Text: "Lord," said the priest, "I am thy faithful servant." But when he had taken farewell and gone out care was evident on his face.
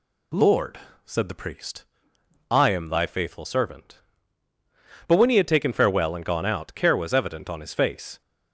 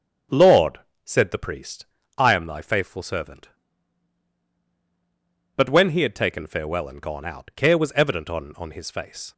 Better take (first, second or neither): first